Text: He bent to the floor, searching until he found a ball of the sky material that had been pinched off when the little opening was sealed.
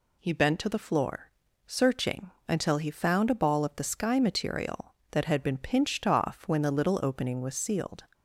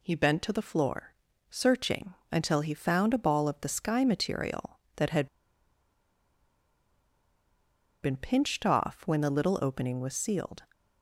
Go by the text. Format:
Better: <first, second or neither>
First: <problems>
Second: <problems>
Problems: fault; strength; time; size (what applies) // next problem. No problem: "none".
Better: first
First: pauses between "searching" and "until"; slight; at 2.3 s; 0.18 s long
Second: pauses between "searching" and "until"; slight; at 2.1 s; 0.18 s long // pauses between "had" and "been"; strong; at 5.2 s; 2.7 s long